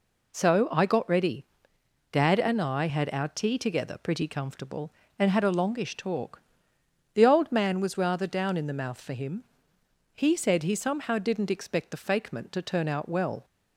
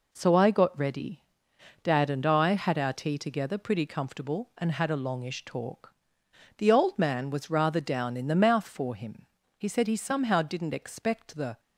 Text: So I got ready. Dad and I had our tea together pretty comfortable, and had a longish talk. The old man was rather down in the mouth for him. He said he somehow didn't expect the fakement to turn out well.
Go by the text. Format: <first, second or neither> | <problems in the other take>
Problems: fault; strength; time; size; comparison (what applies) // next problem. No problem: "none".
first | stops before "fakement to turn out well"; at 11.5 s